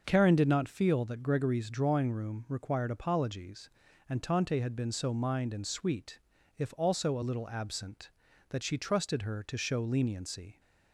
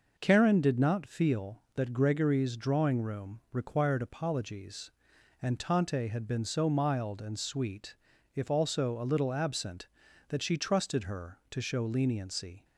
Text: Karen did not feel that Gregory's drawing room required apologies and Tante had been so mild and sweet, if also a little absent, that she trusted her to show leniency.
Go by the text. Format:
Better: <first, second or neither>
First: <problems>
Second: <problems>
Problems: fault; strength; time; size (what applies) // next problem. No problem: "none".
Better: second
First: starts louder than the rest; noticeable; until 1.0 s; 6 dB // says "mind" for "mild"; at 5.1 s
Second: none